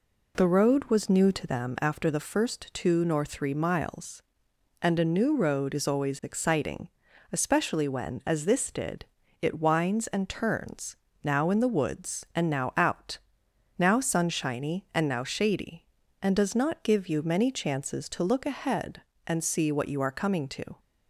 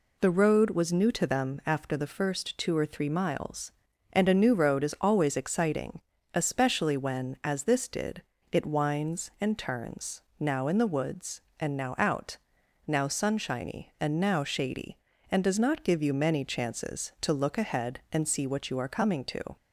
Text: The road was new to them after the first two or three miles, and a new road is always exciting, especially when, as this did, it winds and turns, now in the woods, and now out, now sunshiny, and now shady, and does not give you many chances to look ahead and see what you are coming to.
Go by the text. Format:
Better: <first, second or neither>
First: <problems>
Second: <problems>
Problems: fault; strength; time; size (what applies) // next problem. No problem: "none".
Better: second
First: says "nor" for "or"; at 3.0 s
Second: none